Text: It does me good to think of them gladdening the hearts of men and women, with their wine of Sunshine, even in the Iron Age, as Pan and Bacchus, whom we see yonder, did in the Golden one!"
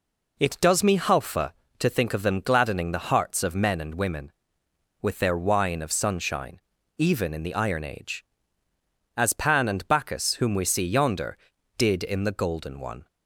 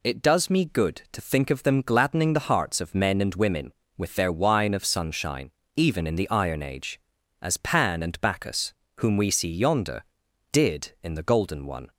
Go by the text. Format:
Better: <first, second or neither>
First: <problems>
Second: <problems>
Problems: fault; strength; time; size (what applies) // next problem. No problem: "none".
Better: second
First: says "halfa" for "good"; at 0.9 s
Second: none